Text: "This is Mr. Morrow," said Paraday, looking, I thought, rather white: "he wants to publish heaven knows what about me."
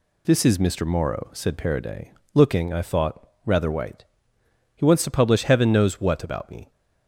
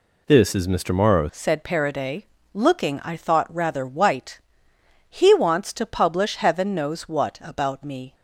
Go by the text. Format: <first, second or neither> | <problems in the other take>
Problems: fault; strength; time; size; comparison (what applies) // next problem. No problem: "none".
first | changes voice at "said"; from 1.3 s on; 6.8 s long